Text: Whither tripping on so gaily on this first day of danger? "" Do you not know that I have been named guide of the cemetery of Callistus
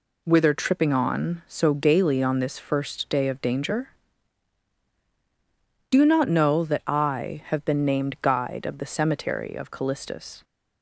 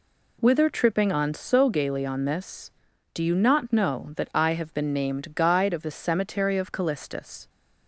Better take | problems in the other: first | skips "first day of danger"; at 2.8 s

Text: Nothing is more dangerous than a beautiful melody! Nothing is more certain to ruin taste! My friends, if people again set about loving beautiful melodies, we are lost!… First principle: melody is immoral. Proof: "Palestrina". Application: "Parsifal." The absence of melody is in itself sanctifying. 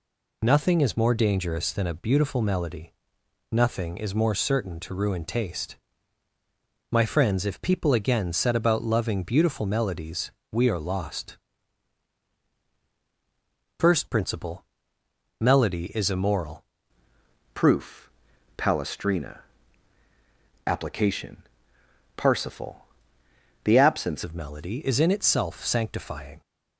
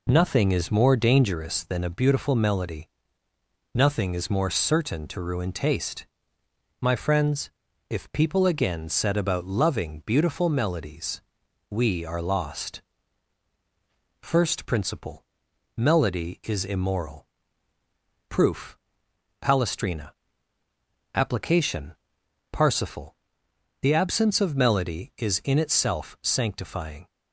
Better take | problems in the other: second | changes voice from "Proof" to "absence"; from 17.5 to 24.2 s; 6.7 s long

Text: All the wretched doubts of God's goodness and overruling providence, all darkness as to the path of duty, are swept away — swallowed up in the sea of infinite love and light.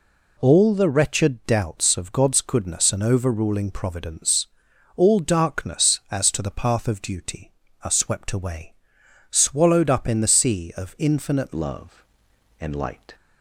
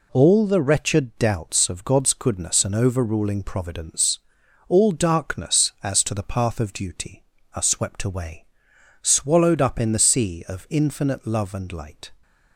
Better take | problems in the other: second | changes voice at "love"; from 11.5 s on; 1.6 s long

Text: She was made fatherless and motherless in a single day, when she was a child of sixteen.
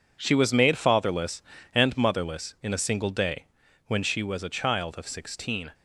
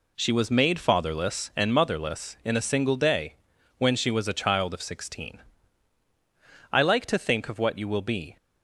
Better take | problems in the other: first | goes on to say "I like to think of what you will be"; from 6.7 s on; 1.6 s long

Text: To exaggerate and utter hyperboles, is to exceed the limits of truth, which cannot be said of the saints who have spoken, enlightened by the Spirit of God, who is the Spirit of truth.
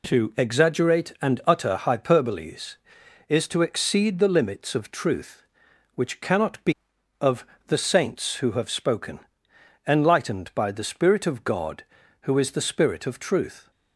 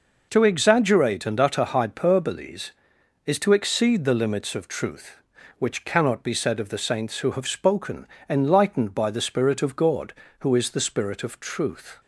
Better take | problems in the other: second | skips "said"; at 6.9 s // pauses between "of" and "the"; slight; at 7.4 s; 0.22 s long

